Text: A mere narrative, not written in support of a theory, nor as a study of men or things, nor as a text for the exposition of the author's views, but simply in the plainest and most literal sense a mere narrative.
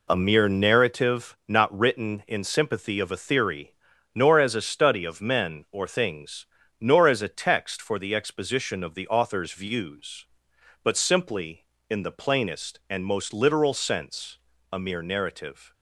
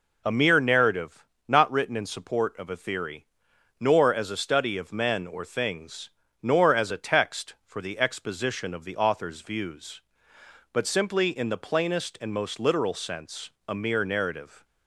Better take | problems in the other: second | says "sympathy" for "support"; at 2.4 s // pauses between "sense" and "a"; slight; at 14.3 s; 0.34 s long; slight in the second

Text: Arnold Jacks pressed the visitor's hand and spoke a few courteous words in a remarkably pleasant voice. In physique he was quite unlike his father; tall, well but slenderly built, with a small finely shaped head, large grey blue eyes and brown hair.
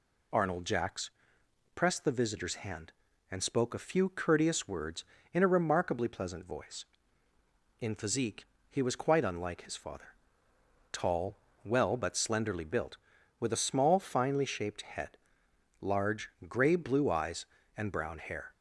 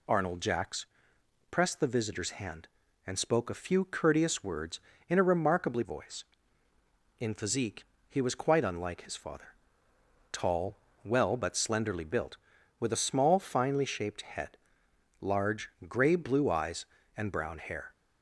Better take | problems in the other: first | pauses between "Jacks" and "pressed"; noticeable; at 0.8 s; 0.66 s long; noticeable in the first // skips "pleasant"; at 5.8 s // pauses between "physique" and "he"; slight; at 7.8 s; 0.24 s long; slight in the first // pauses between "large" and "grey"; slight; at 15.6 s; 0.20 s long; slight in the first

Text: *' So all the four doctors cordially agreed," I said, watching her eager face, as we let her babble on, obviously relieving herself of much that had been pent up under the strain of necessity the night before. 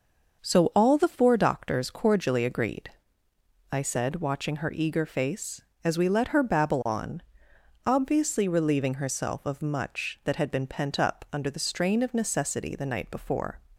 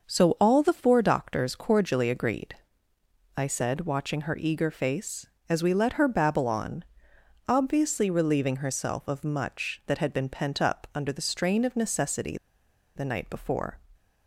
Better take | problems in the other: first | starts louder than the rest; until 1.1 s; 6 dB; also in the first // pauses between "necessity" and "the"; noticeable; at 12.3 s; 0.58 s long

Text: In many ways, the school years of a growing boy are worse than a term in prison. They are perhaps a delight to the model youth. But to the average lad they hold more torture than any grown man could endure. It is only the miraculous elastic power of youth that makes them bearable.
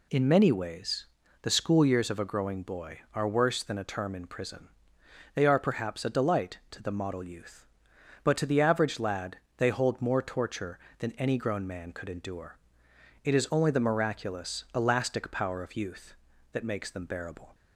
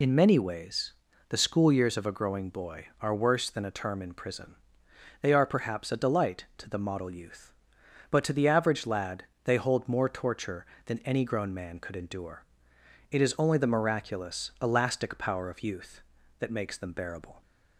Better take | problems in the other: first | loses the start of "In"; at 0.0 s; 35 ms // pauses between "lad" and "they"; slight; at 9.2 s; 0.22 s long; slight in the first

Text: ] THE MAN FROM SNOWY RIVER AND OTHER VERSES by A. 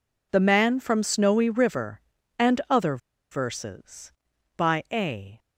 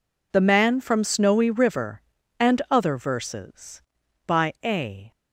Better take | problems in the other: second | pauses between "OTHER" and "VERSES"; slight; at 2.9 s; 0.33 s long

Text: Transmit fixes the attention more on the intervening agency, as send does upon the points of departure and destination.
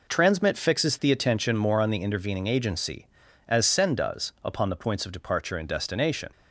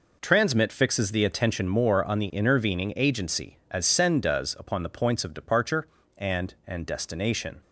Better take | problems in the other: first | says "and" twice; at 6.6 s

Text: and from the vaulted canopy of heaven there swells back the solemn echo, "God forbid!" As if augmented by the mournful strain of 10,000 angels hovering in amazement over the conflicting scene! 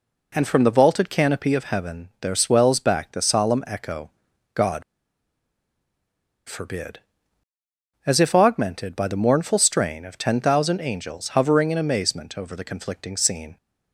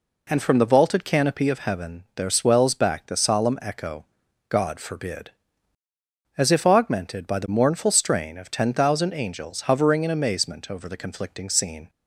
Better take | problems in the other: second | pauses between "God" and "forbid"; strong; at 4.8 s; 1.6 s long

